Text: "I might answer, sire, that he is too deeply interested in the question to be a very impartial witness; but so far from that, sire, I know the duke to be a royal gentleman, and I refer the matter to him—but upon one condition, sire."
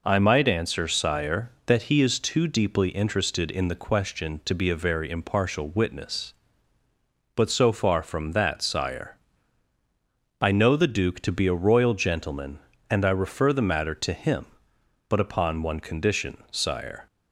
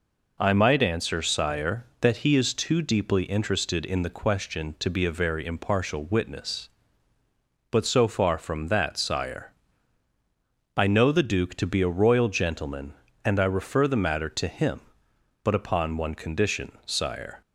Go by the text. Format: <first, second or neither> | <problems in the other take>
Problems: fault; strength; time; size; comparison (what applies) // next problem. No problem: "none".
neither | none